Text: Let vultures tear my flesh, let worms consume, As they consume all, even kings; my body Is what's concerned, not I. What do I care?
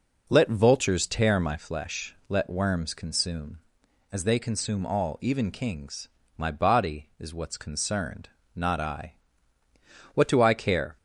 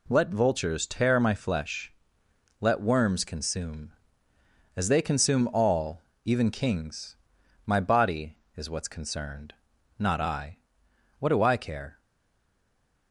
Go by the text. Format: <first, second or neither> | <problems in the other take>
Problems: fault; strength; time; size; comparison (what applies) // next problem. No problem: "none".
first | stays silent after the last word; from 11.9 s on; 1.2 s long